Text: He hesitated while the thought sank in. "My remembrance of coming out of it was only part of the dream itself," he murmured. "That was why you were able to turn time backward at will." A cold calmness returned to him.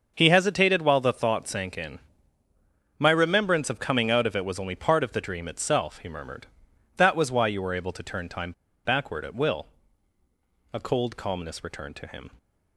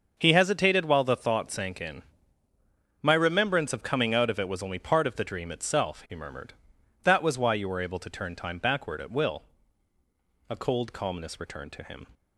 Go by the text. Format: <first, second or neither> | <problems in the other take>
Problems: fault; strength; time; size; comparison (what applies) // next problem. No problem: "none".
second | starts louder than the rest; until 1.1 s; 6.5 dB; also in the second // pauses between "time" and "backward"; slight; at 8.5 s; 0.33 s long